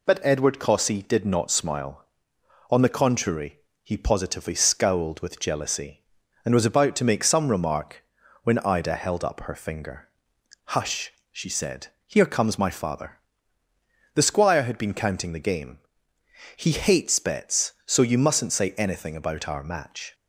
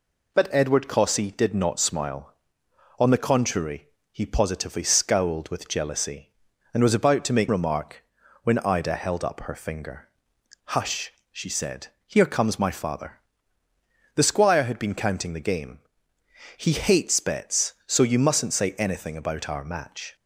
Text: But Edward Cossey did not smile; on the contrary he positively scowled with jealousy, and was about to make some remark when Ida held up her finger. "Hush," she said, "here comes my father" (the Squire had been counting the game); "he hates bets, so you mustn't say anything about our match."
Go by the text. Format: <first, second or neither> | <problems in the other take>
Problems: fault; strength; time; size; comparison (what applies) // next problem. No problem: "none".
first | pauses between "contrary" and "he"; slight; at 3.8 s; 0.24 s long; slight in the first // skips "some"; at 7.4 s // pauses between "remark" and "when"; at 8.0 s; 0.40 s long; also in the first